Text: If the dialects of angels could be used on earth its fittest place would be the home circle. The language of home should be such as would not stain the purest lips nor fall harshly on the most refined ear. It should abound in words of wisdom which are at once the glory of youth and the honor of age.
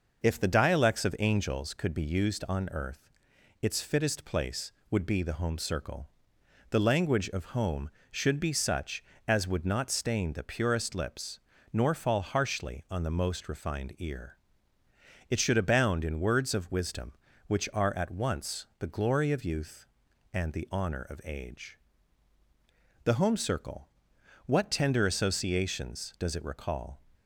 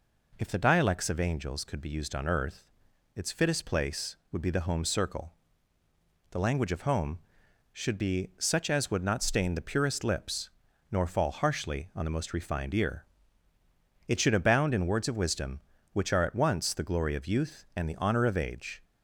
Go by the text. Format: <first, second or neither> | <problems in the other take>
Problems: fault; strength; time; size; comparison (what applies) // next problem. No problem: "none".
second | pauses between "earth" and "its"; noticeable; at 3.0 s; 0.54 s long; noticeable in the second // pauses between "lips" and "nor"; slight; at 11.3 s; 0.34 s long; also in the second // goes on to say "The home circle what tender associations does it recall"; strong; from 23.0 s on; 3.9 s long